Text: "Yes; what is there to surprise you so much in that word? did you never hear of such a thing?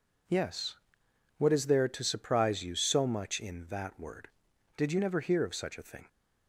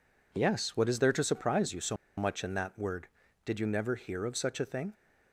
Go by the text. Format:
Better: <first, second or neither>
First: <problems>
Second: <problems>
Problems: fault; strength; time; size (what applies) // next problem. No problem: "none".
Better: first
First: none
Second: pauses between "so" and "much"; slight; at 1.9 s; 0.21 s long